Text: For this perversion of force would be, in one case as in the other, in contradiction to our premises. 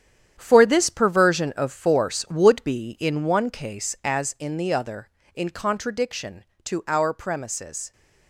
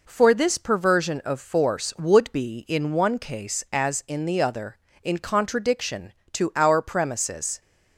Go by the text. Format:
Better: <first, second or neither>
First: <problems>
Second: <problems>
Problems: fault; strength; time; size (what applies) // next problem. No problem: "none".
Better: second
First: gets quieter; strong; throughout; 10 dB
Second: none